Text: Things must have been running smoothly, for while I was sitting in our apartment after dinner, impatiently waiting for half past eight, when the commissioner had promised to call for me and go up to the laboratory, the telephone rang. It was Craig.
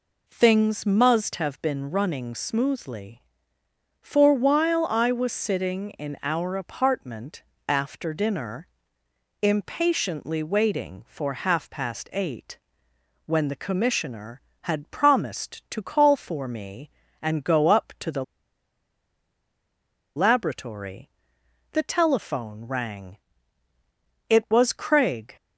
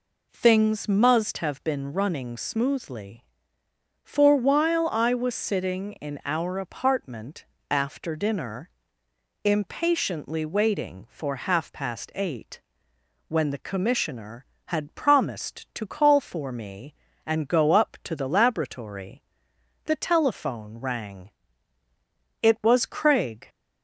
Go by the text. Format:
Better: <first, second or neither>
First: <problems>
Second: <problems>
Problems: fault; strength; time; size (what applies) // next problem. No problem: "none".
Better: second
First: pauses between "apartment" and "after"; slight; at 7.4 s; 0.24 s long // pauses between "the" and "laboratory"; strong; at 18.2 s; 1.9 s long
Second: pauses between "apartment" and "after"; slight; at 7.4 s; 0.24 s long